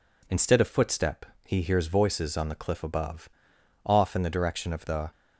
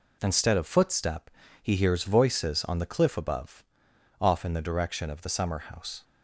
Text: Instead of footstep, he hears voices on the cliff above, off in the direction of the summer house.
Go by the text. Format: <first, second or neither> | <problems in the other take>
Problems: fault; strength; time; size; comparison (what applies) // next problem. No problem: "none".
second | stops before "summer house"; at 5.1 s